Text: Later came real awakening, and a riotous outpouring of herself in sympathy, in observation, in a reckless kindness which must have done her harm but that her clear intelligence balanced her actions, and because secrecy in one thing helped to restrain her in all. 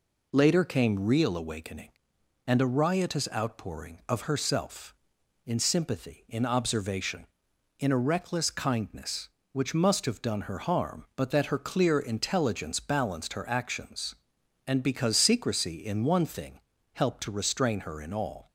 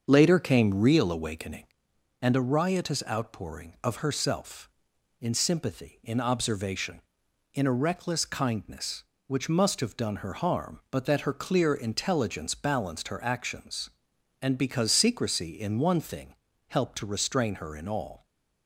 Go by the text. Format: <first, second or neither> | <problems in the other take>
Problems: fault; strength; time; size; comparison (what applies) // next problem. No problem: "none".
first | starts louder than the rest; until 1.8 s; 7 dB // pauses between "thing" and "helped"; slight; at 16.3 s; 0.32 s long; slight in the first